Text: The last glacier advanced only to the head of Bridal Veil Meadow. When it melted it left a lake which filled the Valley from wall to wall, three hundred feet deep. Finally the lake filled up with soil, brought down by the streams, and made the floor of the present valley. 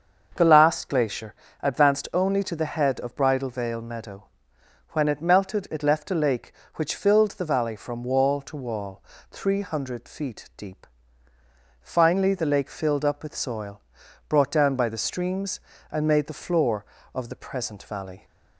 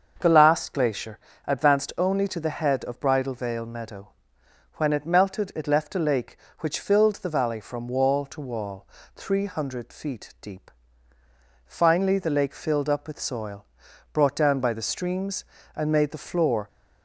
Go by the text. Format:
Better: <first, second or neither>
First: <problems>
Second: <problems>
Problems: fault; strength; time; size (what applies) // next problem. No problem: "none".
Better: first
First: starts louder than the rest; until 1.3 s; 6.5 dB // pauses between "glacier" and "advanced"; slight; at 1.3 s; 0.26 s long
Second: starts louder than the rest; until 1.2 s; 6.5 dB // pauses between "glacier" and "advanced"; slight; at 1.1 s; 0.26 s long // stops before "of the present valley"; at 16.6 s